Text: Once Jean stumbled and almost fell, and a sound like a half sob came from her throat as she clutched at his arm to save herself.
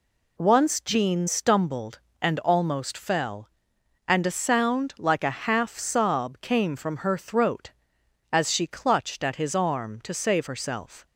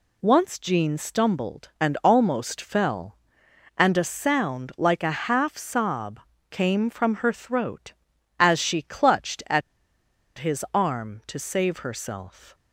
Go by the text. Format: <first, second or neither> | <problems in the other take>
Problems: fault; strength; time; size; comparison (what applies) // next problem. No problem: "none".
first | pauses between "sob" and "came"; slight; at 6.2 s; 0.30 s long // pauses between "at" and "his"; noticeable; at 9.6 s; 0.77 s long